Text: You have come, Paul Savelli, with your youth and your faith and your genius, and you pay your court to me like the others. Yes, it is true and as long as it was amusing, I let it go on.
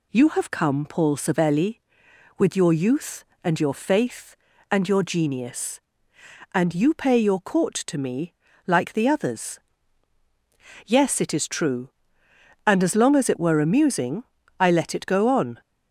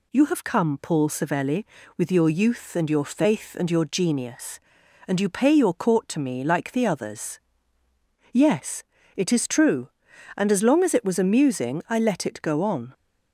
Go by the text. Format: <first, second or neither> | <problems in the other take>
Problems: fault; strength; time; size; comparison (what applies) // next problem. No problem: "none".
second | pauses between "me" and "like"; slight; at 8.3 s; 0.34 s long // says "were" for "was"; at 13.3 s